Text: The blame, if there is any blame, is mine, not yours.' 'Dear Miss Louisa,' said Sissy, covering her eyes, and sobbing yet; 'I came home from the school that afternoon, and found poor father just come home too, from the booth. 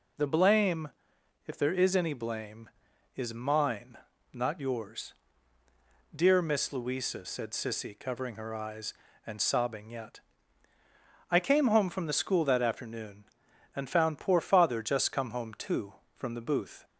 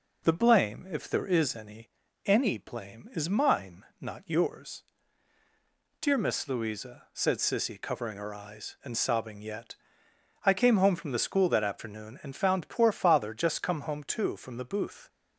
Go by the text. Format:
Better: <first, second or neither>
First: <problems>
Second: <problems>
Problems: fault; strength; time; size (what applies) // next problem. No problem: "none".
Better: first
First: none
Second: says "any" twice; at 2.2 s